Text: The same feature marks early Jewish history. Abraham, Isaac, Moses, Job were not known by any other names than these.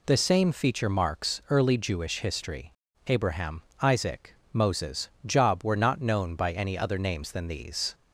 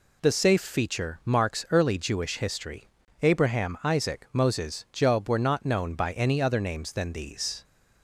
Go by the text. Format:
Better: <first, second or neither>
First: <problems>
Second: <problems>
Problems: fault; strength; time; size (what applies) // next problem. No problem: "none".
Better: first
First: none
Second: says "safe" for "same"; at 0.3 s